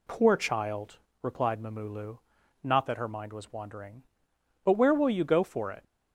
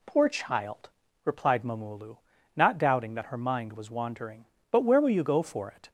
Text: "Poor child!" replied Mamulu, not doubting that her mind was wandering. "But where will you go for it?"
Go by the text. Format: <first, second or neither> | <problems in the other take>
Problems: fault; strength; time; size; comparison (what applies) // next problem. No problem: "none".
second | skips "doubting"; at 2.8 s